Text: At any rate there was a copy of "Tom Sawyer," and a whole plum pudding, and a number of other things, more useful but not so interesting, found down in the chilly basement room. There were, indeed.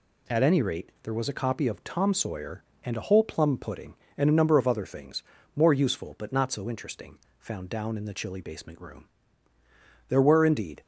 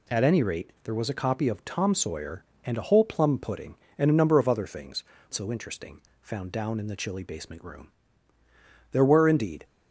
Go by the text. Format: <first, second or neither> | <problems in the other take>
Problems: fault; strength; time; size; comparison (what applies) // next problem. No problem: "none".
first | skips "more useful but not"; at 5.1 s